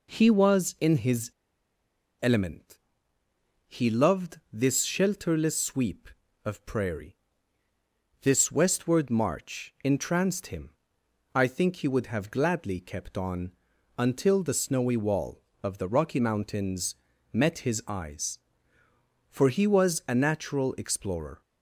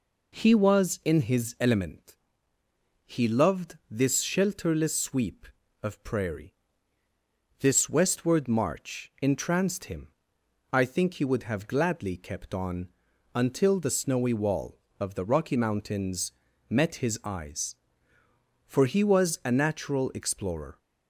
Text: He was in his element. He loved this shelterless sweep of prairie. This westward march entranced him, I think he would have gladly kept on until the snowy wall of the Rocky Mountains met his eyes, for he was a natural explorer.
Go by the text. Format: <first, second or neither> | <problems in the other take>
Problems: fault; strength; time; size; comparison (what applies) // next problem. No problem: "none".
second | pauses between "his" and "element"; noticeable; at 1.2 s; 0.93 s long // pauses between "on" and "until"; noticeable; at 13.5 s; 0.48 s long; noticeable in the second // pauses between "Mountains" and "met"; at 16.9 s; 0.38 s long; also in the second